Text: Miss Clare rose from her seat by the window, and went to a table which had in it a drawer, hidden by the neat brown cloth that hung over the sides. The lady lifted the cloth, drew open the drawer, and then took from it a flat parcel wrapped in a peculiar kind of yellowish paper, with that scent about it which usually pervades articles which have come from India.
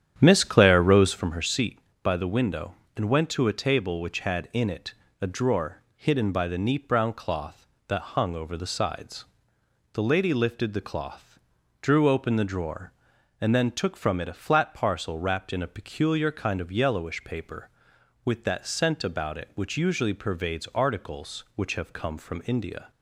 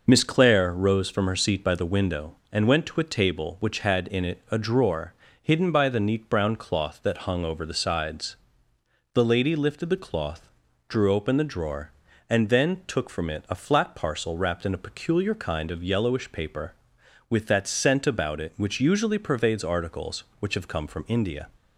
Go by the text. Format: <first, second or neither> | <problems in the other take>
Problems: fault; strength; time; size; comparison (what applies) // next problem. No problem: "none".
second | starts louder than the rest; strong; until 1.3 s; 9.5 dB // pauses between "it" and "a"; slight; at 4.9 s; 0.26 s long